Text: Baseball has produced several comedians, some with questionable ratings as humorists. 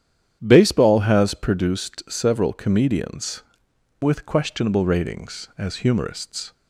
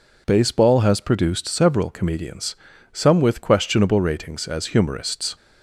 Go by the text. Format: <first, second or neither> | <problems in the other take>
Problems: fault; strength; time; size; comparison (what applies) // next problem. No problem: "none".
second | starts louder than the rest; strong; until 1.4 s; 9.5 dB // skips "some"; at 3.7 s